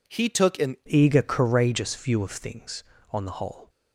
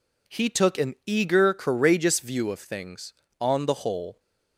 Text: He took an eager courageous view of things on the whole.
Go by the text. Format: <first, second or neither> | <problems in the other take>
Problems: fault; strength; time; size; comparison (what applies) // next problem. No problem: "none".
second | changes voice at "eager"; from 0.8 s on; 2.8 s long